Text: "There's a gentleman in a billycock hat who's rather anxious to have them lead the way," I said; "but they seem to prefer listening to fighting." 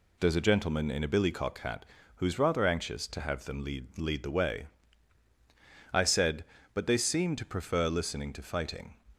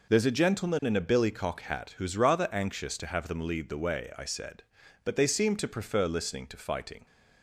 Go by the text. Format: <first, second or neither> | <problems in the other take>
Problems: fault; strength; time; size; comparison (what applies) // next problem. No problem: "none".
second | pauses between "hat" and "who's"; slight; at 1.8 s; 0.30 s long // says "lead" twice; at 3.9 s